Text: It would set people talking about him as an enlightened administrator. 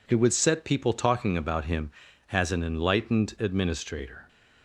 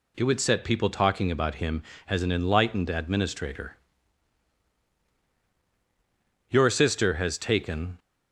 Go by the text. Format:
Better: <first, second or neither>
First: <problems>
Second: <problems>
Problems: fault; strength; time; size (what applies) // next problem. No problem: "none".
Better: first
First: none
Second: goes on to say "Your sister has taken"; from 6.5 s on; 1.4 s long